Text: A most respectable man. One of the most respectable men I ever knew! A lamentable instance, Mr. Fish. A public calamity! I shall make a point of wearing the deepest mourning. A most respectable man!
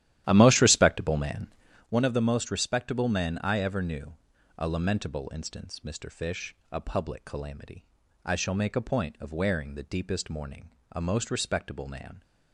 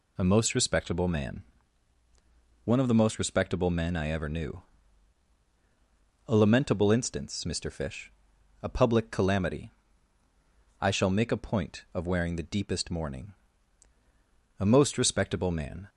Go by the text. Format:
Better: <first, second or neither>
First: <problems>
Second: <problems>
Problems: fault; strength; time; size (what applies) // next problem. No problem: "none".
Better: second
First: starts louder than the rest; strong; until 1.9 s; 12.5 dB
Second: none